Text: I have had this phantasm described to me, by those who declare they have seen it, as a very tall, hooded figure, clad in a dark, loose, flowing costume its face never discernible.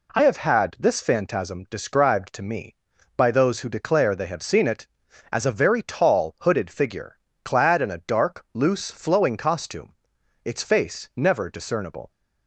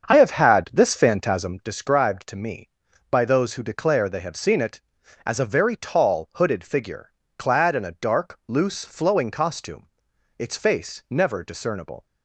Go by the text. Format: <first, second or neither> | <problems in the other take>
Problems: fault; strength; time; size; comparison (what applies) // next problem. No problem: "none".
first | starts louder than the rest; strong; until 1.8 s; 7 dB // pauses between "costume" and "its"; noticeable; at 9.8 s; 0.48 s long; noticeable in the first